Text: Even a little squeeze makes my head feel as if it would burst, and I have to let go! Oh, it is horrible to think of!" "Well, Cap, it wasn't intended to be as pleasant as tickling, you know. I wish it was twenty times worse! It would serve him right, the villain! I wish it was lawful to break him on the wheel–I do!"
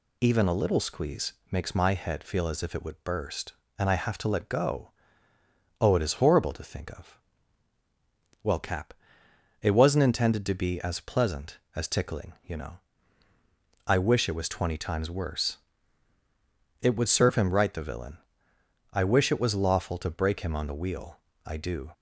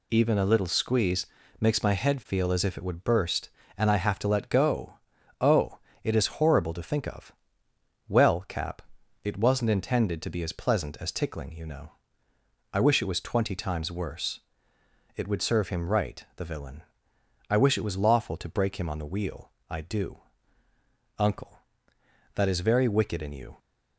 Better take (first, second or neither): first